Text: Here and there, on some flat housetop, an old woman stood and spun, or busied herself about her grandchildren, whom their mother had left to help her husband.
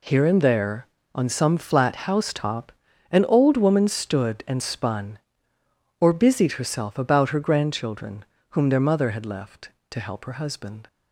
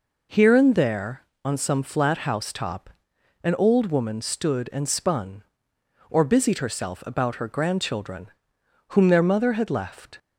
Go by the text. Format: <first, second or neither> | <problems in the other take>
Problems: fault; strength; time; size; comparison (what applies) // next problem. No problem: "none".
first | stops before "to help her husband"; at 10.1 s